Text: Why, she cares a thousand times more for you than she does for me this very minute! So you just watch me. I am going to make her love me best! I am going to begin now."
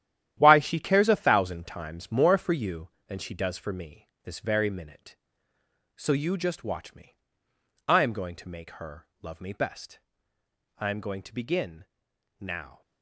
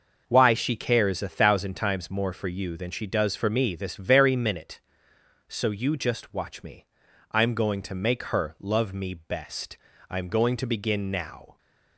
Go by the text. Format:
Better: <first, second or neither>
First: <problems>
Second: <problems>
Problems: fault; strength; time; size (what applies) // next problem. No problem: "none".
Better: second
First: gets quieter; strong; throughout; 10.5 dB // pauses between "me" and "this"; slight; at 4.0 s; 0.16 s long // pauses between "begin" and "now"; noticeable; at 11.8 s; 0.54 s long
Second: none